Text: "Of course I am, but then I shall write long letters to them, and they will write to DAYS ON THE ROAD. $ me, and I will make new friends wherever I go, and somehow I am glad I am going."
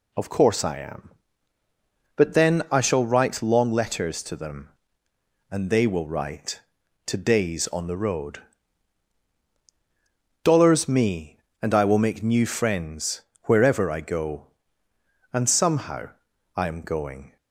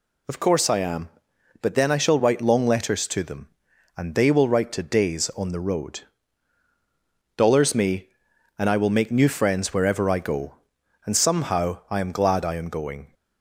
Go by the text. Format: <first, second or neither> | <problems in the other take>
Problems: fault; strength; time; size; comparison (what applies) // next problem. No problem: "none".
second | pauses between "friends" and "wherever"; slight; at 13.2 s; 0.22 s long // pauses between "somehow" and "I"; at 16.1 s; 0.44 s long // skips "glad I am"; at 16.8 s